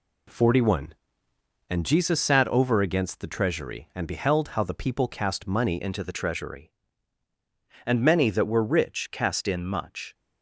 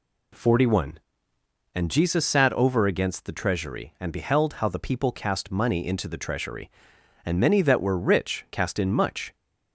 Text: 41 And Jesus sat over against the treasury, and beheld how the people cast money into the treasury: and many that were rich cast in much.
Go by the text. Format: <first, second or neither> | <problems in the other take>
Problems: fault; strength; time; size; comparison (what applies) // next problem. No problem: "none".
second | changes voice at "into"; from 5.7 s on; 4.4 s long